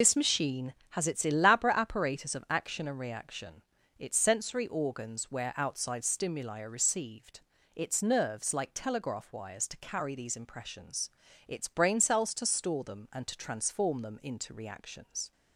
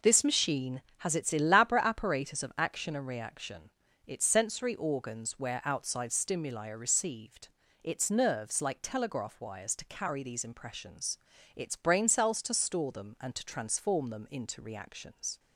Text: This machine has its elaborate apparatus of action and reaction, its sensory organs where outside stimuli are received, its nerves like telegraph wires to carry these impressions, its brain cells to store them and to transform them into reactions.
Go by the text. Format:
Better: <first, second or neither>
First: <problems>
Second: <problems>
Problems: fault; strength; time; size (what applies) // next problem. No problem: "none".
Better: second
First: loses the start of "This"; at 0.0 s; 50 ms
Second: none